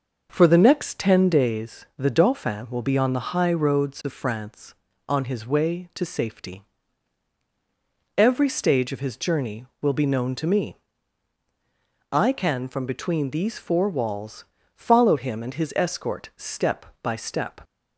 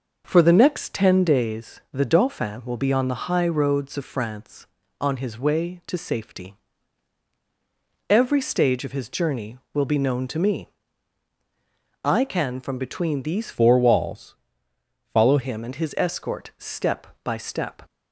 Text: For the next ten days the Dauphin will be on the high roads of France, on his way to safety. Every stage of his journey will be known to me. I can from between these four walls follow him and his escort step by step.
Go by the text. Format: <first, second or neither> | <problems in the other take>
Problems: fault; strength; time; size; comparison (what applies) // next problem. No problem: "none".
first | changes voice from "four" to "follow"; from 13.5 to 15.3 s; 1.8 s long // pauses between "walls" and "follow"; noticeable; at 14.3 s; 0.74 s long; slight in the first